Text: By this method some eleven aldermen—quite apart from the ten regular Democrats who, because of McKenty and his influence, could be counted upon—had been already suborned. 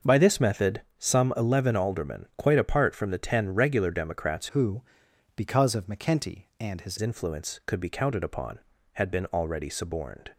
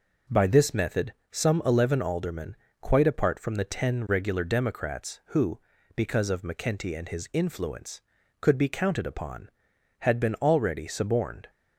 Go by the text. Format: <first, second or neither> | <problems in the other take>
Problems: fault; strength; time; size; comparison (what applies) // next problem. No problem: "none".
second | starts louder than the rest; until 1.2 s; 6 dB // pauses between "method" and "some"; slight; at 0.8 s; 0.16 s long; slight in the second // changes voice from "who" to "his"; from 4.5 to 6.9 s; 2.4 s long